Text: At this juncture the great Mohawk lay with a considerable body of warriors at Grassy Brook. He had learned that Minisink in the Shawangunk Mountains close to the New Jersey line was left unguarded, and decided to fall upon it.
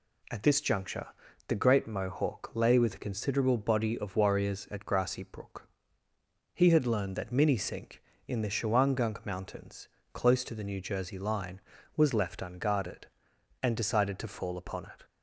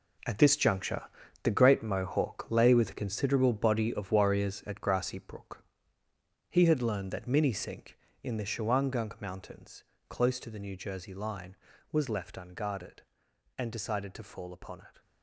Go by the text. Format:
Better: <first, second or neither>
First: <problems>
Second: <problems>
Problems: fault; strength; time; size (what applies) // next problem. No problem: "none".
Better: first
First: pauses between "juncture" and "the"; at 1.0 s; 0.40 s long // pauses between "Mountains" and "close"; slight; at 9.8 s; 0.26 s long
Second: gets quieter; strong; throughout; 11.5 dB // pauses between "juncture" and "the"; at 1.0 s; 0.40 s long // pauses between "Mountains" and "close"; slight; at 9.8 s; 0.26 s long